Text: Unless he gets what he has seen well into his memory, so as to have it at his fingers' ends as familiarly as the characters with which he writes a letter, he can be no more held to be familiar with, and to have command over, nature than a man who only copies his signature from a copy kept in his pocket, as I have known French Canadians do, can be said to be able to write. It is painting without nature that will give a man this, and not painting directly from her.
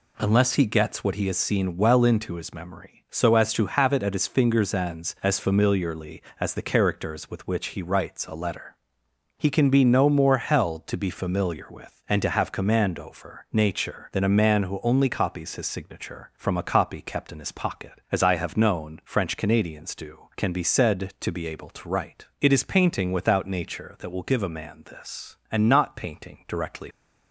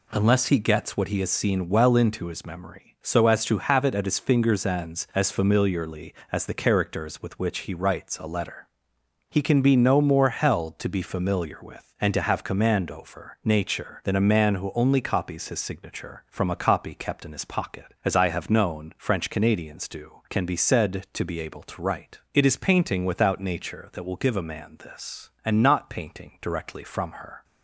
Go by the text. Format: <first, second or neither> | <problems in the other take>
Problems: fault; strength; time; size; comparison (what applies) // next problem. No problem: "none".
second | stops before "from her"; at 26.9 s